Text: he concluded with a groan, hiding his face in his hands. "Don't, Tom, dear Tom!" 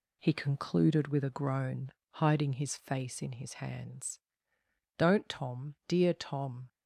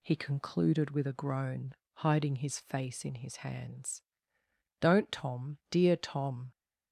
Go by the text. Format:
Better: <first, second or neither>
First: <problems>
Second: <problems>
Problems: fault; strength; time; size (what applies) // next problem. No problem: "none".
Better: second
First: gets quieter; noticeable; throughout; 5 dB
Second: none